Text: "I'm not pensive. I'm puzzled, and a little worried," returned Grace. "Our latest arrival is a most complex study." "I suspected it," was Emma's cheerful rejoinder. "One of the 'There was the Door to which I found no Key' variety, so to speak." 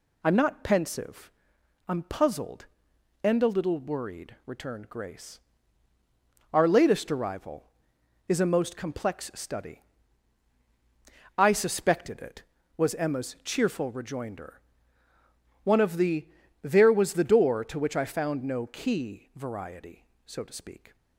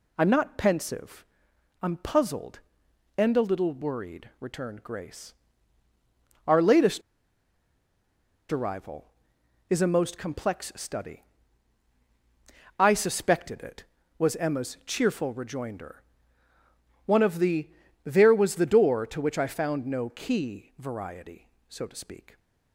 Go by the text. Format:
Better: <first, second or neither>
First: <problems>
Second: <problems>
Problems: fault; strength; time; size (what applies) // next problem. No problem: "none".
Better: first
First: pauses between "the" and "There"; slight; at 16.2 s; 0.34 s long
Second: pauses between "latest" and "arrival"; strong; at 7.0 s; 1.5 s long // pauses between "the" and "There"; slight; at 17.6 s; 0.34 s long